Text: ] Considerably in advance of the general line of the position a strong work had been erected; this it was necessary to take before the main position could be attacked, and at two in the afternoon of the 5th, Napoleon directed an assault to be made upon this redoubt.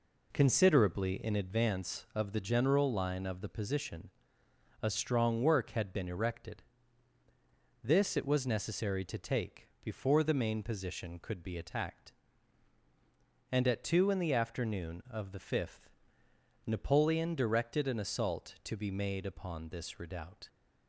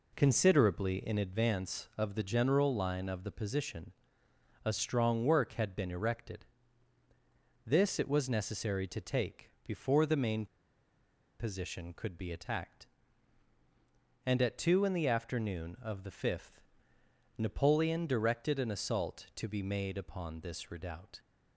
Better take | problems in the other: first | pauses between "position" and "a"; noticeable; at 3.9 s; 0.72 s long; noticeable in the first // pauses between "take" and "before"; slight; at 9.4 s; 0.16 s long; slight in the first // pauses between "main" and "position"; noticeable; at 10.4 s; 0.93 s long

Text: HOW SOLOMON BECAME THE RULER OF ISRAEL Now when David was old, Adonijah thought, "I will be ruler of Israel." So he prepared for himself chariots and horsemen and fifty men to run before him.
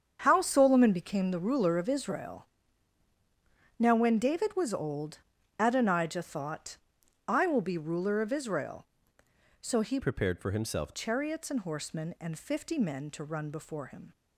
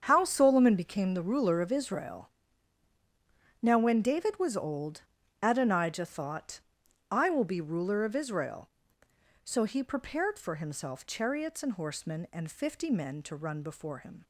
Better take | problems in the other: second | starts louder than the rest; strong; until 1.2 s; 7.5 dB; strong in the second // pauses between "ISRAEL" and "Now"; strong; at 2.4 s; 1.3 s long; strong in the second // changes voice from "prepared" to "himself"; from 9.9 to 10.9 s; 1.0 s long

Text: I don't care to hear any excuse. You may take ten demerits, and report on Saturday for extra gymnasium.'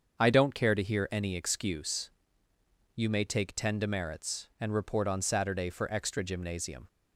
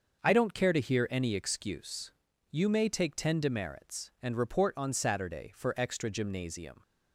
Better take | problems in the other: neither | starts louder than the rest; the same in both

